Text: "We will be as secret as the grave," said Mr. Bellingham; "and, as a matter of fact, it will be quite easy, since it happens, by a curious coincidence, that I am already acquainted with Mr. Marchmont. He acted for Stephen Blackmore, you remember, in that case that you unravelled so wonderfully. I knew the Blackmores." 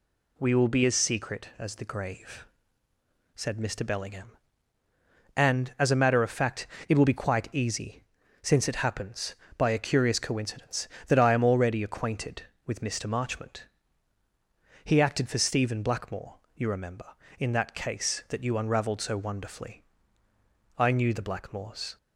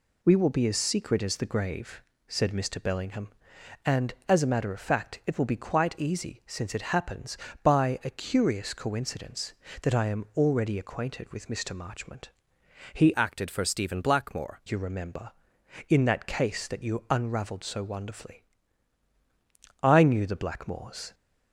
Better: first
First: none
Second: changes voice from "acted" to "Blackmore"; from 13.1 to 14.6 s; 1.5 s long

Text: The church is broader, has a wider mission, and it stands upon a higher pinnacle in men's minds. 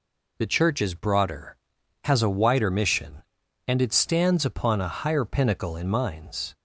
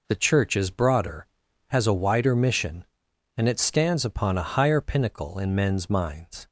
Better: second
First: skips "men's"; at 5.8 s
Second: none

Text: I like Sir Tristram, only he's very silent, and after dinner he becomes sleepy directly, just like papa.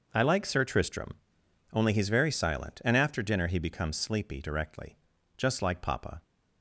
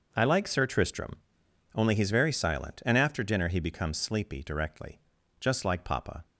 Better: neither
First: none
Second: none

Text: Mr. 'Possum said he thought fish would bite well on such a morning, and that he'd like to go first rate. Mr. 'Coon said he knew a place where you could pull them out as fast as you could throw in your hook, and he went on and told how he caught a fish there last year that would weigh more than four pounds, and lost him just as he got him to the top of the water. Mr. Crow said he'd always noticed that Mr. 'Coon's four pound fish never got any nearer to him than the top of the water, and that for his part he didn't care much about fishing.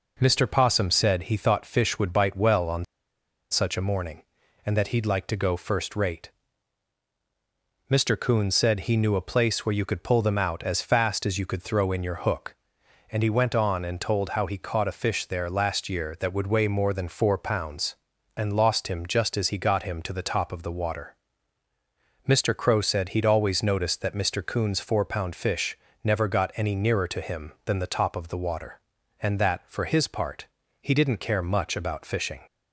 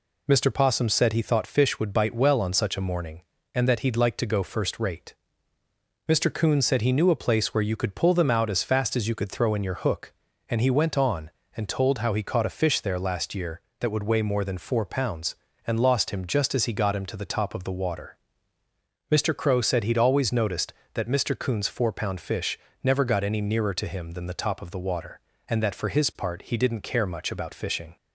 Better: second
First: pauses between "on" and "such"; noticeable; at 2.8 s; 0.67 s long // pauses between "fish" and "never"; slight; at 25.7 s; 0.26 s long // pauses between "part" and "he"; slight; at 30.4 s; 0.34 s long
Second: pauses between "fish" and "never"; slight; at 22.5 s; 0.24 s long

